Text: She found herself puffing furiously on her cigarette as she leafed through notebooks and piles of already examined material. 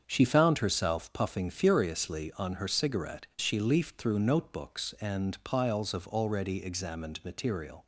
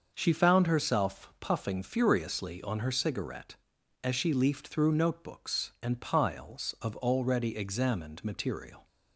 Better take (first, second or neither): second